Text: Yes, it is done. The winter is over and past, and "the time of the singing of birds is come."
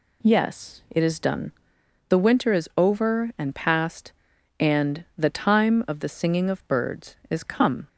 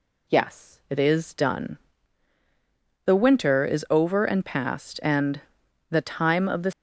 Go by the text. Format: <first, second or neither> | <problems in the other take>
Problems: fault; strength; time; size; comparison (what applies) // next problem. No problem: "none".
first | pauses between "and" and "the"; noticeable; at 5.3 s; 0.50 s long // stops before "singing of birds is come"; at 6.7 s